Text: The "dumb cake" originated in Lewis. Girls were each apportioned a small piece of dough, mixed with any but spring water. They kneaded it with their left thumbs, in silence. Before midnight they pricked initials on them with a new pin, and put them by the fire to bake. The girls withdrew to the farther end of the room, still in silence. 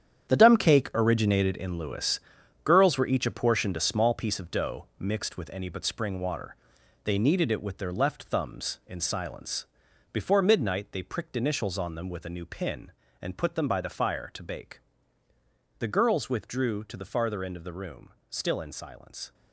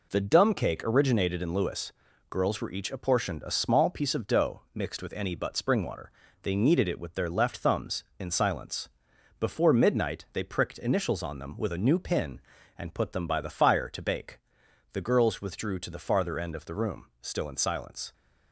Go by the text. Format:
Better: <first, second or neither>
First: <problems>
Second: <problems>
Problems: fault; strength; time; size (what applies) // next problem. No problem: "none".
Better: second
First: gets quieter; strong; throughout; 11 dB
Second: none